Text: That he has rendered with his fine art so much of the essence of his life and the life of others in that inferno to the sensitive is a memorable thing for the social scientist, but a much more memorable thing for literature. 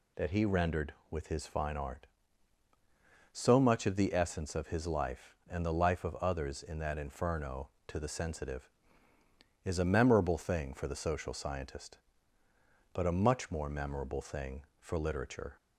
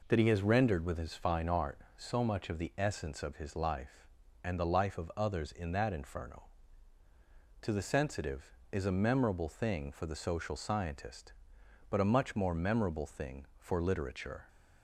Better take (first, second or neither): second